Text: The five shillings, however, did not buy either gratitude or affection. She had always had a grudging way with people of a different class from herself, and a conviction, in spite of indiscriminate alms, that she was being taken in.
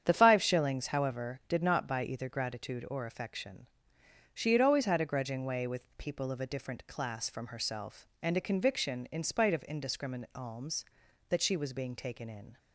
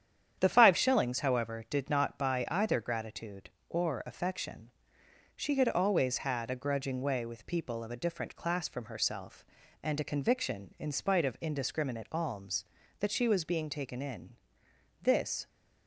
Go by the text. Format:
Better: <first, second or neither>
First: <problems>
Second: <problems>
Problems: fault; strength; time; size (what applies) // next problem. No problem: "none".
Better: first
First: starts louder than the rest; strong; until 1.0 s; 8.5 dB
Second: starts louder than the rest; strong; until 1.4 s; 9 dB // goes on to say "This"; slight; from 15.0 s on; 0.46 s long